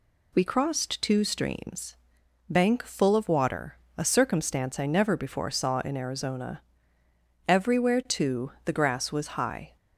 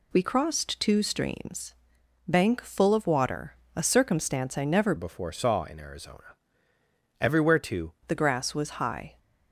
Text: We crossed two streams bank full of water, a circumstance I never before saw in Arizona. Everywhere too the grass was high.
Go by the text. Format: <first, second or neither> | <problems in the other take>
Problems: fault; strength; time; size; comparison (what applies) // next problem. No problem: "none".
first | pauses between "streams" and "bank"; noticeable; at 1.7 s; 0.54 s long; noticeable in the first // changes voice from "before" to "too"; from 4.9 to 7.9 s; 3.0 s long